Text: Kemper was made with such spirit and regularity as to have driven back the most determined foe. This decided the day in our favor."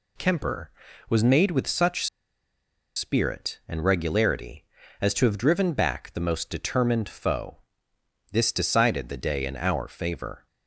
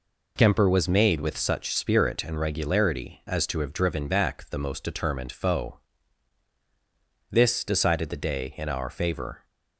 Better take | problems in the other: second | pauses between "such" and "spirit"; noticeable; at 2.0 s; 0.89 s long

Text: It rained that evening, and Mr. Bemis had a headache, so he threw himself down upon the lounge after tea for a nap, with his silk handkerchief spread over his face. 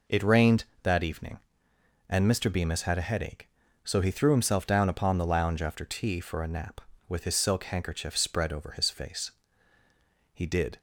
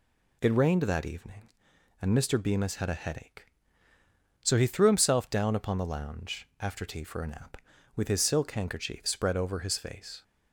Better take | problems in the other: second | goes on to say "He did"; slight; from 10.3 s on; 0.46 s long

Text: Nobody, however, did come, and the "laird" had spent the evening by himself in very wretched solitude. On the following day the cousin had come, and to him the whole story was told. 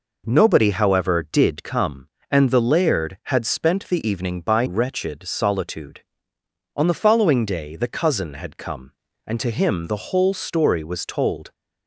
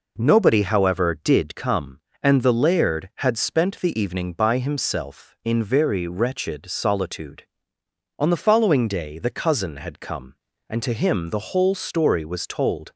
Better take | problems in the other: second | skips "himself in very"; at 4.6 s

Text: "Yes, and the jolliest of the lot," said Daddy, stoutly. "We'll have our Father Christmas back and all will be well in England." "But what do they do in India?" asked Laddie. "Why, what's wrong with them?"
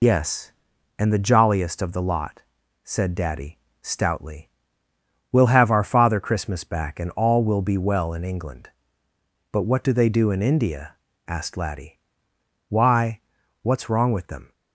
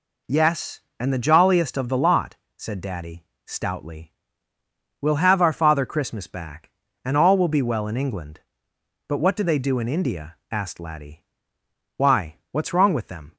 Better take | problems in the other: second | loses the start of "Yes"; at 0.0 s; 40 ms

